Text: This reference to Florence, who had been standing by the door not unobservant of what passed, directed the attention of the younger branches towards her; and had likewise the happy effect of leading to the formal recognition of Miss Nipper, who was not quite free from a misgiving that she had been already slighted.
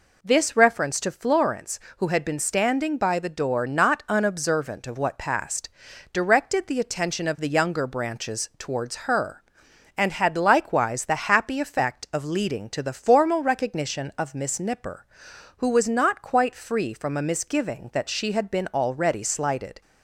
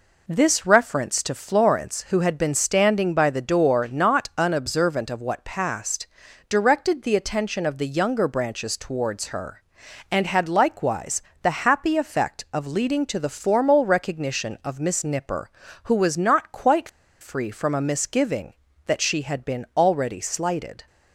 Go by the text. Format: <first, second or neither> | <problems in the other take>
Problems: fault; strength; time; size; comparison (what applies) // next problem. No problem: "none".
first | pauses between "likewise" and "the"; slight; at 11.2 s; 0.22 s long // pauses between "quite" and "free"; slight; at 16.8 s; 0.31 s long